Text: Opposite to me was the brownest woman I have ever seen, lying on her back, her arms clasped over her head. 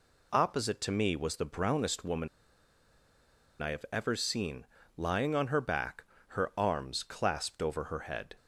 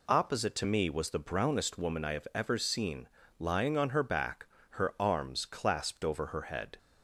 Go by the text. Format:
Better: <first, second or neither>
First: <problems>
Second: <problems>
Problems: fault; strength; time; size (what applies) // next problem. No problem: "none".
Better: second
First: pauses between "woman" and "I"; strong; at 2.2 s; 1.3 s long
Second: none